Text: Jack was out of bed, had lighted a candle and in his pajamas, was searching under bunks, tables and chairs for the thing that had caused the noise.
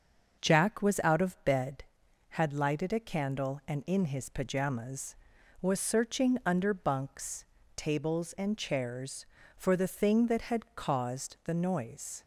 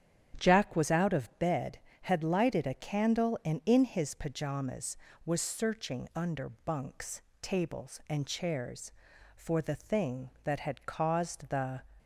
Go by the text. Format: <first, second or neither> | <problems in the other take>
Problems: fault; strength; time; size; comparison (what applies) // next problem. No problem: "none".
first | starts louder than the rest; strong; until 1.4 s; 9.5 dB; also in the first // stops before "noise"; at 11.9 s